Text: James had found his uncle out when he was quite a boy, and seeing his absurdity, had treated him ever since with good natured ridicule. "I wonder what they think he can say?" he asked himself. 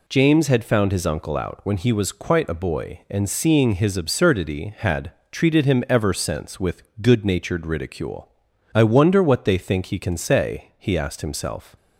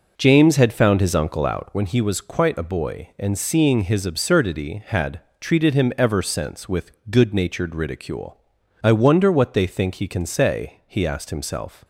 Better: first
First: pauses between "had" and "treated"; slight; at 5.1 s; 0.20 s long // pauses between "with" and "good"; slight; at 6.8 s; 0.18 s long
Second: starts louder than the rest; noticeable; until 1.8 s; 5 dB // pauses between "had" and "treated"; slight; at 5.1 s; 0.20 s long // pauses between "with" and "good"; slight; at 6.9 s; 0.18 s long

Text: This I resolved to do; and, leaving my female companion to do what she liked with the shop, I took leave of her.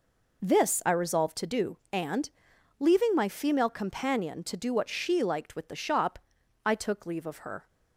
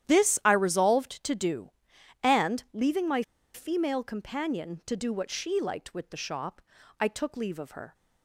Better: first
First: none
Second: starts louder than the rest; strong; until 1.1 s; 11 dB // pauses between "my" and "female"; slight; at 3.2 s; 0.32 s long

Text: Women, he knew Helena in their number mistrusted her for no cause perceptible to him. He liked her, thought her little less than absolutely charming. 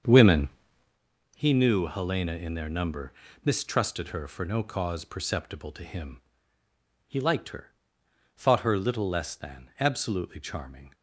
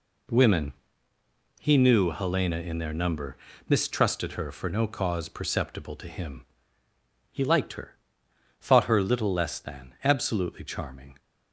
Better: second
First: starts louder than the rest; until 1.0 s; 7 dB // pauses between "number" and "mistrusted"; slight; at 3.1 s; 0.32 s long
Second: pauses between "number" and "mistrusted"; slight; at 3.3 s; 0.32 s long

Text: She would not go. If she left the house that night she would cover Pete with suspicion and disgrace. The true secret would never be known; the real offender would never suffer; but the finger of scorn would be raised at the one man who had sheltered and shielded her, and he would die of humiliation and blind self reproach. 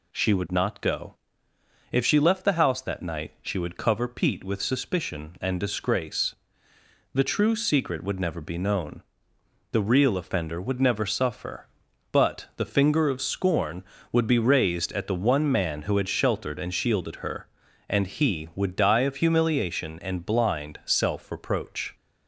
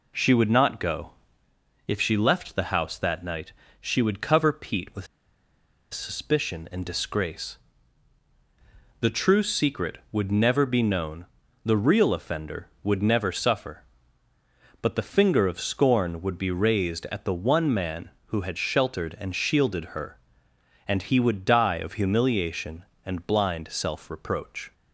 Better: first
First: none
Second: pauses between "night" and "she"; slight; at 3.5 s; 0.30 s long // pauses between "with" and "suspicion"; noticeable; at 5.0 s; 0.86 s long

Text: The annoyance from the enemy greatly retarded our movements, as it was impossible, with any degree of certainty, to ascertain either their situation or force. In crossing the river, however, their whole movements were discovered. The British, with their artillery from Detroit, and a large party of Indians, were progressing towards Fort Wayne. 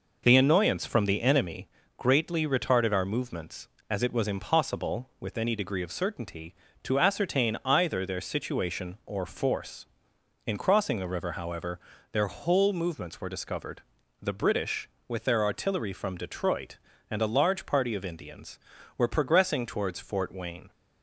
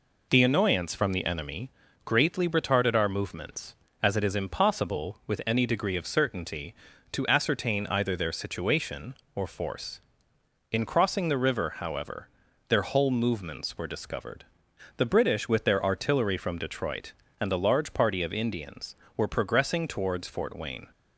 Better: first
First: pauses between "enemy" and "greatly"; slight; at 1.6 s; 0.30 s long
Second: pauses between "enemy" and "greatly"; slight; at 1.7 s; 0.34 s long // says "is" for "was"; at 4.2 s

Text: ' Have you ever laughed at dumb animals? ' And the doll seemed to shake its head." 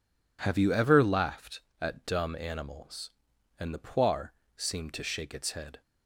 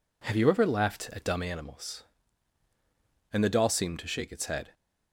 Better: second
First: says "poire" for "doll"; at 3.7 s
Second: none

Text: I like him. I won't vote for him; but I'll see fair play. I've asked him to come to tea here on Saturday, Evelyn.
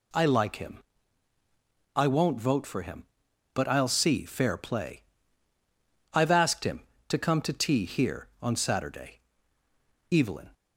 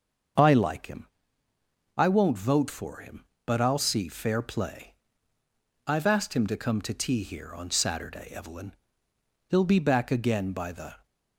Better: first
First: none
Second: starts louder than the rest; until 2.2 s; 6.5 dB // goes on to say "He'll be back again by the"; from 9.4 s on; 1.5 s long

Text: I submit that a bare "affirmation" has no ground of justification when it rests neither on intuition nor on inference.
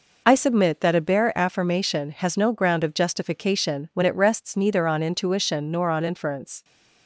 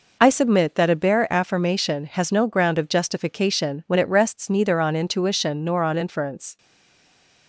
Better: first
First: none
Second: stays silent after the last word; slight; from 6.5 s on; 0.9 s long

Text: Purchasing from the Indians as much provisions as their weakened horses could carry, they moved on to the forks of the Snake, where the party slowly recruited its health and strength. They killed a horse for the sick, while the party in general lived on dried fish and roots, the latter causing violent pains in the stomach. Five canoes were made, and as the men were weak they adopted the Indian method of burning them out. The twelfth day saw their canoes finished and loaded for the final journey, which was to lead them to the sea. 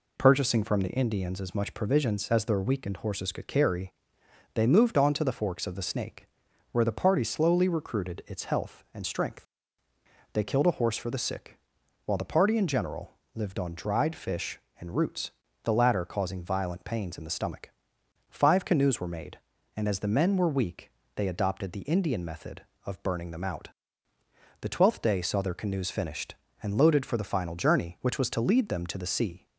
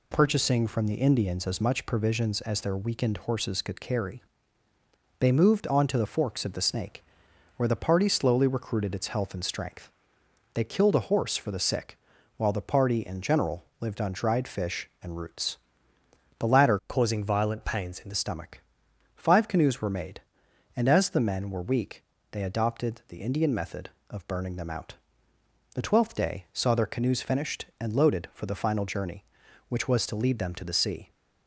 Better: first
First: pauses between "general" and "lived"; slight; at 13.1 s; 0.22 s long // pauses between "weak" and "they"; slight; at 20.9 s; 0.24 s long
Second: pauses between "general" and "lived"; slight; at 13.6 s; 0.16 s long // changes voice from "causing" to "the"; from 16.8 to 18.1 s; 1.3 s long // pauses between "weak" and "they"; slight; at 22.0 s; 0.28 s long

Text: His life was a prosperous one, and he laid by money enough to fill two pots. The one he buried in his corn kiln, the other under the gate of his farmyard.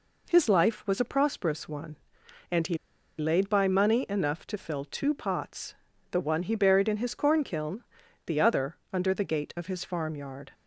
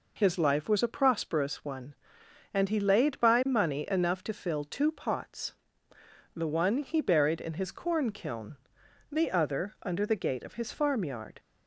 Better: second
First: pauses between "he" and "laid"; at 2.7 s; 0.42 s long // pauses between "other" and "under"; slight; at 8.7 s; 0.16 s long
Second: none

